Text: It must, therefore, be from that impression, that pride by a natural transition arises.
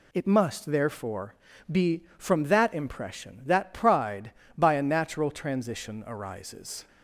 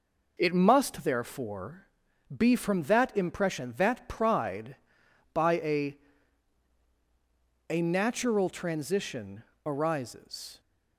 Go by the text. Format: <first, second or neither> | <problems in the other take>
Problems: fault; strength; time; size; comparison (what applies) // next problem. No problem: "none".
first | says "a" twice; at 7.7 s // pauses between "transition" and "arises"; slight; at 9.4 s; 0.24 s long